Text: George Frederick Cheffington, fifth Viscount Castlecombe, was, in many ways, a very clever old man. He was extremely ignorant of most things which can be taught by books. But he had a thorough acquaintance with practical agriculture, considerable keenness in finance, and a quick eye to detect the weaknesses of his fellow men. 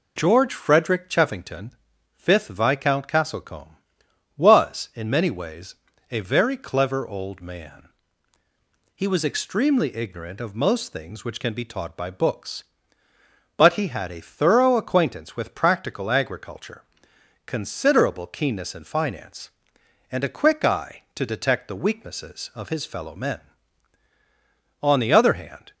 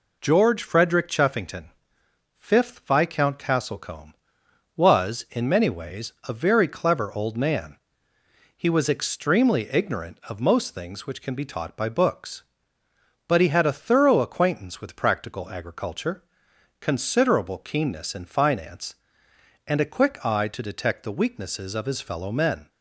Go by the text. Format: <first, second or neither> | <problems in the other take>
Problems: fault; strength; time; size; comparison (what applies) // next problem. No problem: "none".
second | goes on to say "On the other hand"; noticeable; from 24.8 s on; 0.92 s long